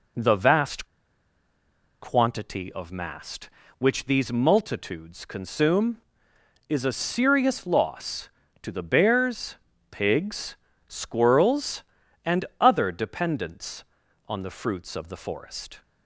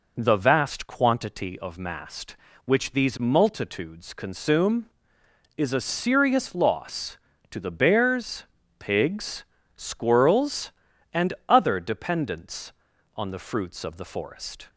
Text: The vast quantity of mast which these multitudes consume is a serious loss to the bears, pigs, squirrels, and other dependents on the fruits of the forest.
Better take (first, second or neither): second